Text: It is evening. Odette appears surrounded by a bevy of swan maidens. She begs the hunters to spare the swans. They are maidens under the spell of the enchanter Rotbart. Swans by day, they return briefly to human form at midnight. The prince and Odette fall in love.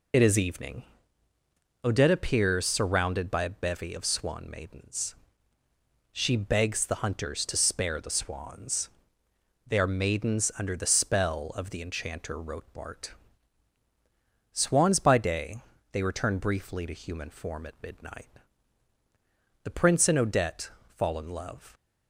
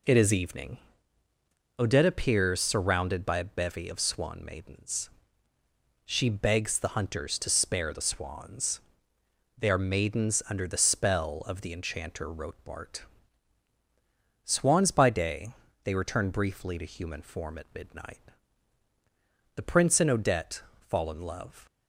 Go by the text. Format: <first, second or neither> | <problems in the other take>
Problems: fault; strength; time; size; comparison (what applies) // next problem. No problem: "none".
second | loses the start of "It"; at 0.1 s; 35 ms // pauses between "Odette" and "fall"; slight; at 20.6 s; 0.18 s long; slight in the second